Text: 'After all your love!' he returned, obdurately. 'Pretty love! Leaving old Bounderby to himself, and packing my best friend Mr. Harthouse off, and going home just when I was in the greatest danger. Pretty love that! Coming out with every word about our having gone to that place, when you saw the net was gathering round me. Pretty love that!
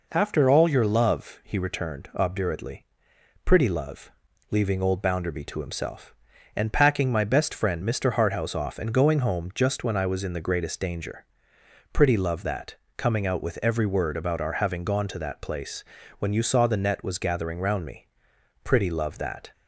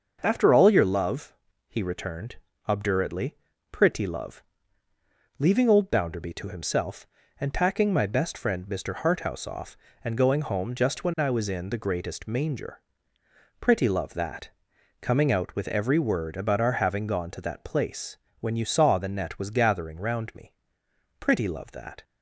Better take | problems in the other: first | starts louder than the rest; until 1.2 s; 6.5 dB // says "manger" for "danger"; at 12.2 s

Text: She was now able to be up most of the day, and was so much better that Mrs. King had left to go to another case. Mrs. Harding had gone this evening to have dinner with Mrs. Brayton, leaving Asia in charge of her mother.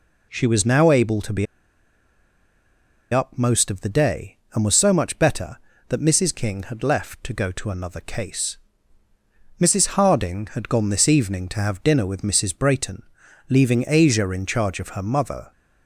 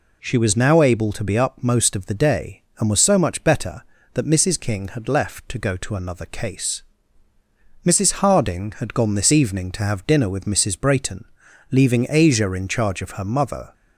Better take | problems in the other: second | pauses between "be" and "up"; strong; at 1.4 s; 1.6 s long

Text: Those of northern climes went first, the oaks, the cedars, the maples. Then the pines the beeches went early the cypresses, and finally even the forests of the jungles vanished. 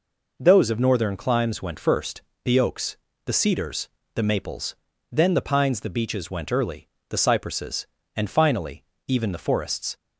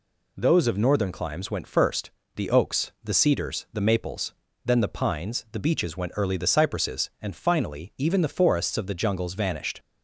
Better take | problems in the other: second | pauses between "early" and "the"; slight; at 6.8 s; 0.18 s long // pauses between "finally" and "even"; slight; at 8.8 s; 0.24 s long // stops before "of the jungles vanished"; at 9.9 s

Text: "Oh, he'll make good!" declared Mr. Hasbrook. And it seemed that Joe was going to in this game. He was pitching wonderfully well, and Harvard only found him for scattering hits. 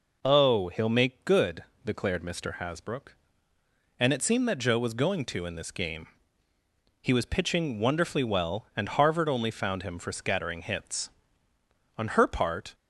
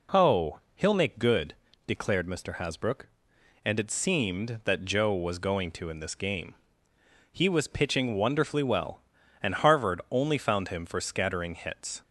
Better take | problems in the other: second | goes on to say "On her part"; noticeable; from 11.9 s on; 0.78 s long

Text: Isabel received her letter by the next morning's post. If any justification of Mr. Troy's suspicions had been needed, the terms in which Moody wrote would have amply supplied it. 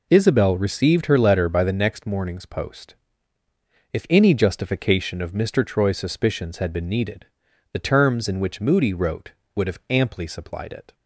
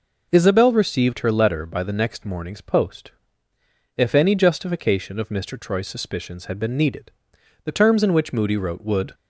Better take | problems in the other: first | stops before "have amply supplied it"; at 9.1 s

